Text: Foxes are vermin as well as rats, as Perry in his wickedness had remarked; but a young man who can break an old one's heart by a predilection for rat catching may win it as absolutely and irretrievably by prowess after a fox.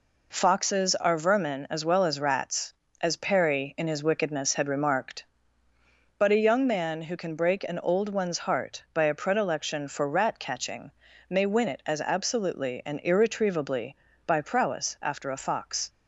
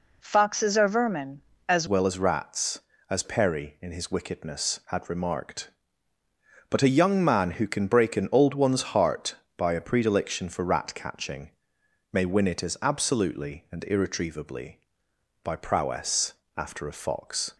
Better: first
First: pauses between "catching" and "may"; at 10.8 s; 0.40 s long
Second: changes voice at "well"; from 1.8 s on; 15.7 s long // pauses between "catching" and "may"; noticeable; at 11.4 s; 0.62 s long // pauses between "prowess" and "after"; slight; at 16.3 s; 0.22 s long

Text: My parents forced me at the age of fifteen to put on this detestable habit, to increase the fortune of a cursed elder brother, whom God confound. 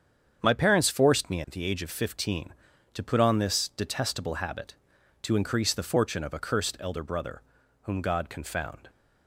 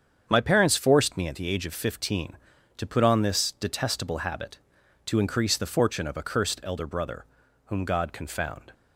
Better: neither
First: starts louder than the rest; strong; until 1.4 s; 7.5 dB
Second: starts louder than the rest; strong; until 1.2 s; 7.5 dB

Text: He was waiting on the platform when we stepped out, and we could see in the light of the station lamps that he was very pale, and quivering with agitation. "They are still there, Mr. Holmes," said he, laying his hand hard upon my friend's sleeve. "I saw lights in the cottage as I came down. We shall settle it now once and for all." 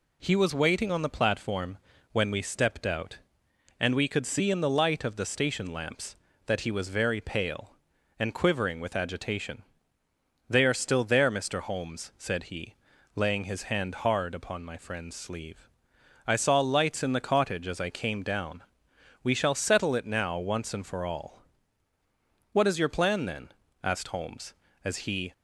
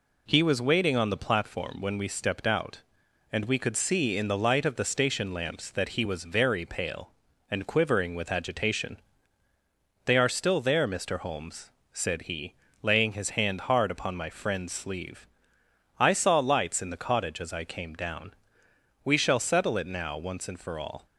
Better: second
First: pauses between "platform" and "when"; slight; at 1.7 s; 0.32 s long // goes on to say "What is your plan then asked Holmes as he"; strong; from 22.5 s on; 2.8 s long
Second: none

